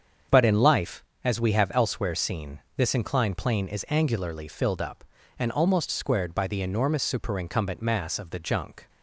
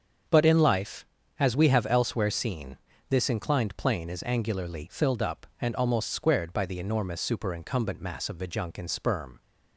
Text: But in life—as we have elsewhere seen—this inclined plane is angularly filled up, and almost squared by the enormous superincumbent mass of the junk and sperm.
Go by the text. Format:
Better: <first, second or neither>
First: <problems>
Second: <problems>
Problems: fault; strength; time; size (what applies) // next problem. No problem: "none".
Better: second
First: starts louder than the rest; strong; until 1.5 s; 7.5 dB // stops before "and sperm"; at 8.8 s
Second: starts louder than the rest; strong; until 1.6 s; 7 dB